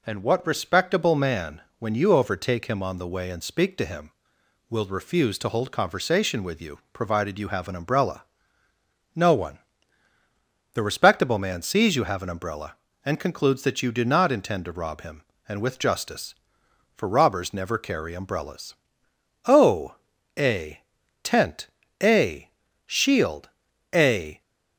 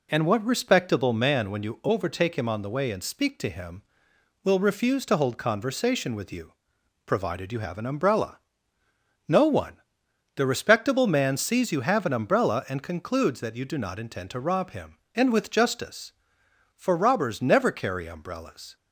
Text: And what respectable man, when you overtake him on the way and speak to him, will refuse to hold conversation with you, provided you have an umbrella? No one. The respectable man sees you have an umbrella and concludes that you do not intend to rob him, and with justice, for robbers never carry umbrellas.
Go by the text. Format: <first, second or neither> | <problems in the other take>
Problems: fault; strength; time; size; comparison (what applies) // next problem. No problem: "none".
second | goes on to say "O a tent a shield a"; strong; from 19.4 s on; 4.9 s long